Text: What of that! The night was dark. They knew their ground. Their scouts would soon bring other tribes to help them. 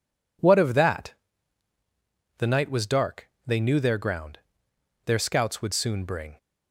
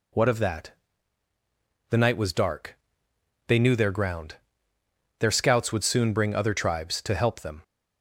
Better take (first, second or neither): second